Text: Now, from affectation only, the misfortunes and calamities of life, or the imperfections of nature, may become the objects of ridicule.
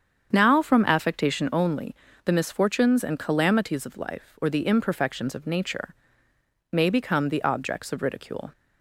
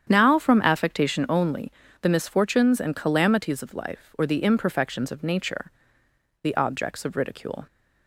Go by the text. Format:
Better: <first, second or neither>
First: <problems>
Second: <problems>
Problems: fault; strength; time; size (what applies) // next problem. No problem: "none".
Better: first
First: starts louder than the rest; strong; until 1.3 s; 7.5 dB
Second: starts louder than the rest; strong; until 1.1 s; 8.5 dB // skips "may become"; at 6.0 s